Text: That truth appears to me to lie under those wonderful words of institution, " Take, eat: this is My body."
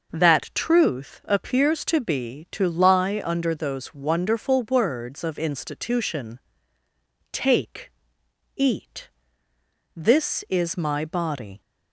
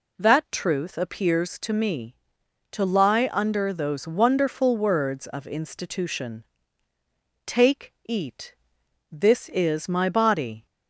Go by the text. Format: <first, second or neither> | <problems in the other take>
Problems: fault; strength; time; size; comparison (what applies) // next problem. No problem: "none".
second | says "be" for "me"; at 2.0 s